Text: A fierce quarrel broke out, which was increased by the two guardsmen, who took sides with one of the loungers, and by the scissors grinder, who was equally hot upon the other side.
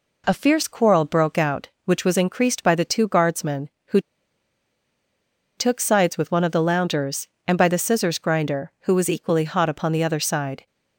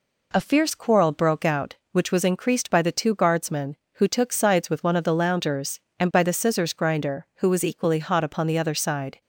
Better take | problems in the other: second | pauses between "who" and "took"; strong; at 4.0 s; 1.5 s long

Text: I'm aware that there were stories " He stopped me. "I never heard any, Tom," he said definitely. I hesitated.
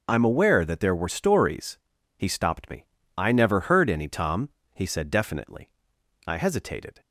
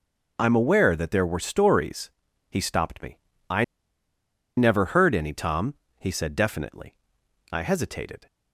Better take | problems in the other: first | pauses between "I" and "never"; noticeable; at 3.6 s; 0.93 s long

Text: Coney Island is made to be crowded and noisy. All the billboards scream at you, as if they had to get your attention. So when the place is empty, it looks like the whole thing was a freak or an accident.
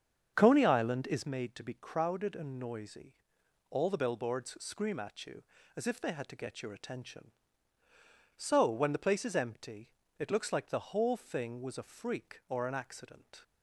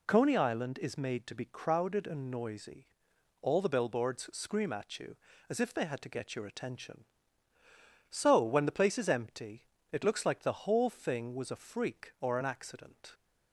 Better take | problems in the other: second | starts louder than the rest; strong; until 1.3 s; 7 dB

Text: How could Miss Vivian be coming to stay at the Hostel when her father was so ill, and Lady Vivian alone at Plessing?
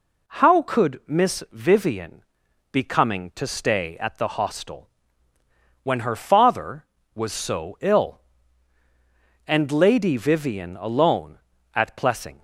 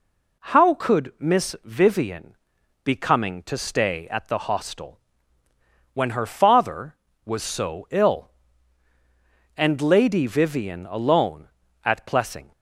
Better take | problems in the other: neither | pauses between "Vivian" and "be"; noticeable; the same in both // pauses between "Hostel" and "when"; noticeable; the same in both

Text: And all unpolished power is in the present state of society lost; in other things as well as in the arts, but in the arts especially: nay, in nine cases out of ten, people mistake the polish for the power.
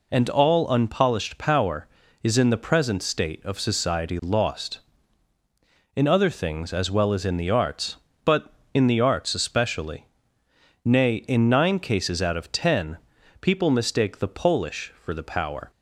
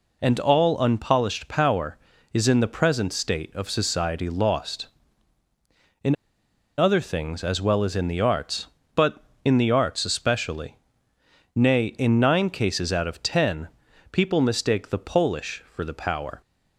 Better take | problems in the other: first | pauses between "in" and "other"; noticeable; at 6.1 s; 0.63 s long

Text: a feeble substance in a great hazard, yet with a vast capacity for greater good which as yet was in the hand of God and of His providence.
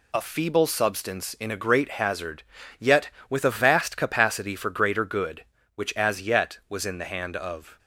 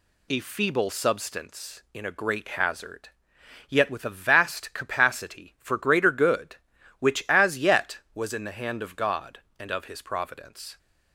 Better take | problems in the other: second | stops before "God and of His providence"; at 7.7 s

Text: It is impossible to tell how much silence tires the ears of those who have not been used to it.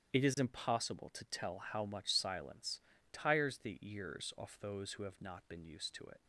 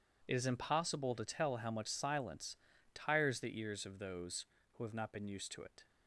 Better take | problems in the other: second | starts louder than the rest; strong; until 1.2 s; 9.5 dB // pauses between "silence" and "tires"; slight; at 2.7 s; 0.32 s long; also in the second // says "off" for "of"; at 4.3 s

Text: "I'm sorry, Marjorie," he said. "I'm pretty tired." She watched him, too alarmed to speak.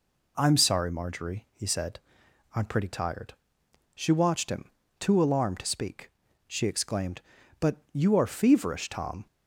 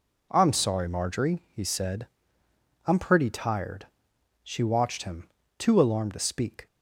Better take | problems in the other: second | goes on to say "She exclaimed But you are feverish Tom"; strong; from 6.4 s on; 2.8 s long

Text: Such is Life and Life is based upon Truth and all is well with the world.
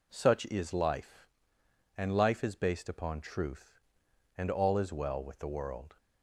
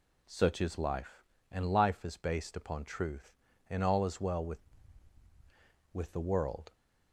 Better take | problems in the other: first | says "with" twice; at 5.9 s

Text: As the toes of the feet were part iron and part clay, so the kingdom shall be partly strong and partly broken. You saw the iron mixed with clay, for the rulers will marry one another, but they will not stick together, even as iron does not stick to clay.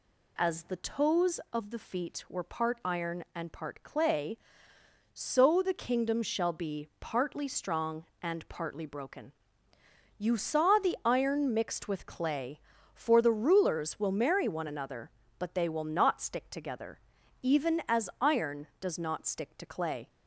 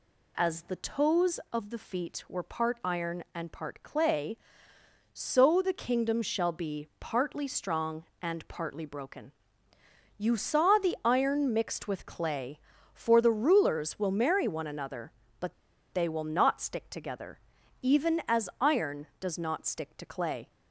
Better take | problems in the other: first | pauses between "but" and "they"; at 15.5 s; 0.40 s long

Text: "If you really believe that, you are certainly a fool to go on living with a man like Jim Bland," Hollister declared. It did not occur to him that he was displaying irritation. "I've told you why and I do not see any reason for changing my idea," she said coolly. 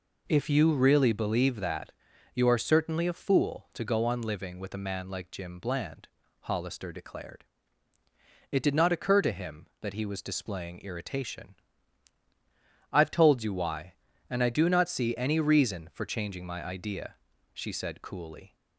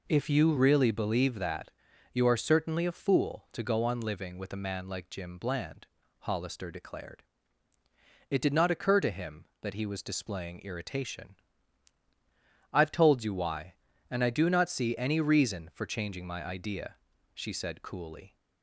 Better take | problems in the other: neither | none

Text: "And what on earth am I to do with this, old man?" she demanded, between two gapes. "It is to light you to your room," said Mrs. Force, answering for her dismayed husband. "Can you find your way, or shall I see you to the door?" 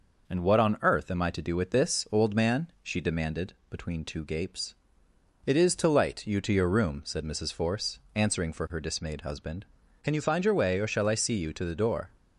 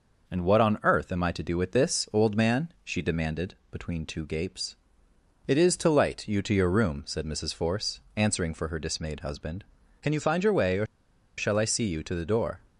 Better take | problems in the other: first | pauses between "or" and "shall"; noticeable; at 10.8 s; 0.51 s long

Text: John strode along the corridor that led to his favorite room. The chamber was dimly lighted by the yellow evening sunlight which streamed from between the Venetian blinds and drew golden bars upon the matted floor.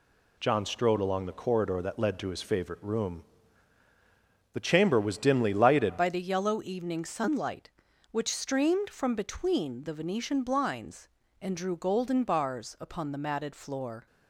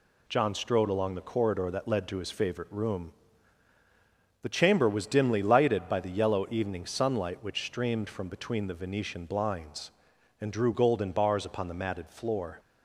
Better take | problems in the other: second | changes voice at "by"; from 5.9 s on; 8.1 s long

